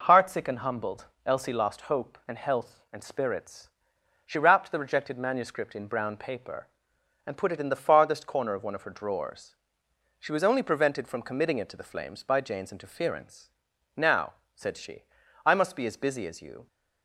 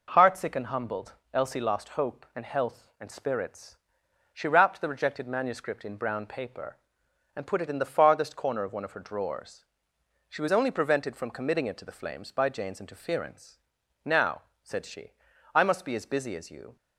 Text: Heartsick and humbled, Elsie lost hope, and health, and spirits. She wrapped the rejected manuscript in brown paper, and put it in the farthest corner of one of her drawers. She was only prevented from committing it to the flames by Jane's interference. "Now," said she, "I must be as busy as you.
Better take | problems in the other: neither | none

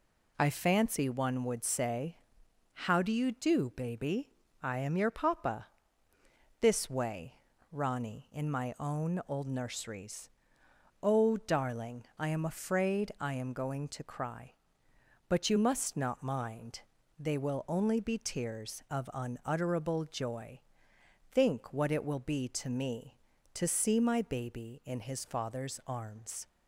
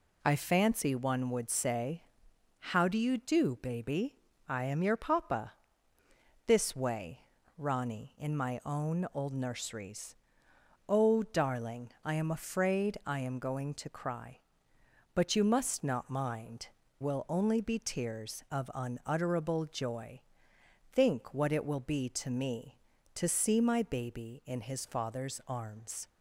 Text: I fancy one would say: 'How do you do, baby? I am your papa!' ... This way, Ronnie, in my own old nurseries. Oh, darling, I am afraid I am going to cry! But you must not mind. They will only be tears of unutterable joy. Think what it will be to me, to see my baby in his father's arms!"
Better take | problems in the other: first | skips "They"; at 16.8 s

